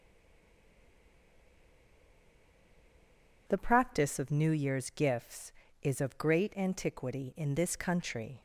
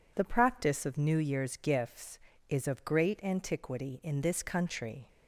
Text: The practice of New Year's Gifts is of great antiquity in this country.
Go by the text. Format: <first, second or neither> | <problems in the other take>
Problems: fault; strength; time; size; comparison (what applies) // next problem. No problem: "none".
second | stays silent before the first word; strong; until 3.4 s; 3.4 s long